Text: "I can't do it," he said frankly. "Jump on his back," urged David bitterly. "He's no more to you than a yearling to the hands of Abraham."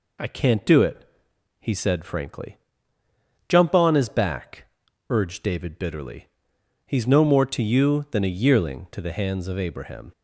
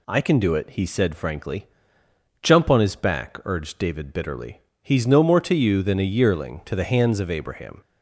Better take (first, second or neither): first